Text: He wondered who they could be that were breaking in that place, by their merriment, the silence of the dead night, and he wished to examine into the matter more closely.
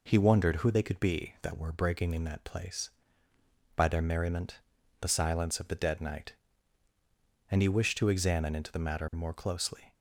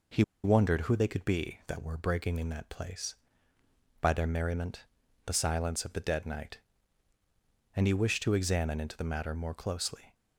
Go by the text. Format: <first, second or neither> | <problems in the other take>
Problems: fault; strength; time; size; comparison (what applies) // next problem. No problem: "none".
first | pauses between "He" and "wondered"; slight; at 0.2 s; 0.21 s long